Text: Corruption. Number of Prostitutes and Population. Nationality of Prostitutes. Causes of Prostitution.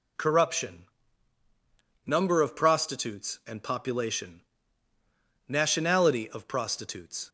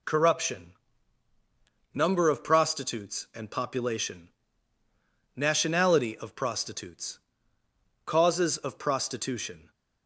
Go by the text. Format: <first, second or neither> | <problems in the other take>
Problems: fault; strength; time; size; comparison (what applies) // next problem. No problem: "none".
second | stops before "Causes of Prostitution"; at 7.2 s